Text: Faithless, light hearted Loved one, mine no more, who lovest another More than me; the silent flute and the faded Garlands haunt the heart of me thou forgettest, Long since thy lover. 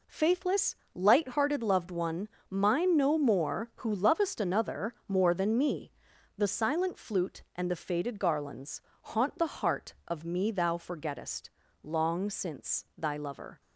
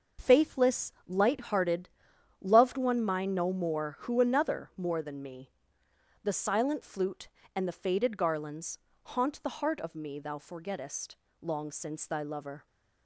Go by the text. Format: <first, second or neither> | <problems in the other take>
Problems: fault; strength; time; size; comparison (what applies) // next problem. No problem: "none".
first | starts louder than the rest; noticeable; until 1.3 s; 6 dB // pauses between "hearted" and "Loved"; noticeable; at 1.8 s; 0.54 s long // skips "lovest"; at 4.1 s // pauses between "Garlands" and "haunt"; slight; at 8.7 s; 0.26 s long; slight in the first